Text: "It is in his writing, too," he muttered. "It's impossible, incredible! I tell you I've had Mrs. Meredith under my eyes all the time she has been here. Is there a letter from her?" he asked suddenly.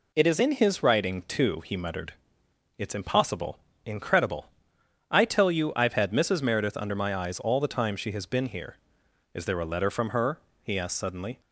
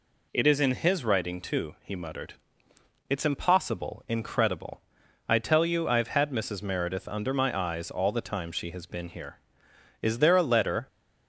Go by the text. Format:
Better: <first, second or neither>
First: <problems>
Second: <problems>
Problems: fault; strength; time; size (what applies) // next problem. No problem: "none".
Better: first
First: none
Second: stops before "from her he asked suddenly"; at 10.8 s